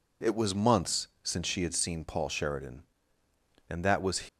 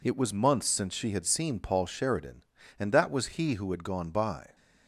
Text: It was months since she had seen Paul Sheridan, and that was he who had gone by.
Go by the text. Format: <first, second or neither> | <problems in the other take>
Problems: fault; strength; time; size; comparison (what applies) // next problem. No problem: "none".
second | pauses between "months" and "since"; slight; at 1.0 s; 0.16 s long // stops before "he who had gone by"; at 4.2 s